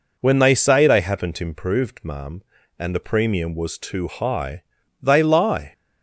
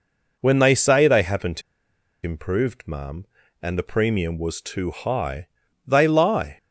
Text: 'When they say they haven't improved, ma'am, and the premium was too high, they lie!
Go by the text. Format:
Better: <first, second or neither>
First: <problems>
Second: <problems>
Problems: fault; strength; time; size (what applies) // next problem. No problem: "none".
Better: first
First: none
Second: pauses between "haven't" and "improved"; noticeable; at 1.6 s; 0.63 s long